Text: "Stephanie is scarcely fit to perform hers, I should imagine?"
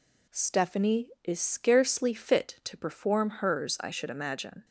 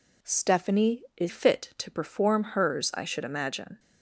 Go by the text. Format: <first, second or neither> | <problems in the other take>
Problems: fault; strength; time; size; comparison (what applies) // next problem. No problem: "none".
first | skips "scarcely"; at 1.2 s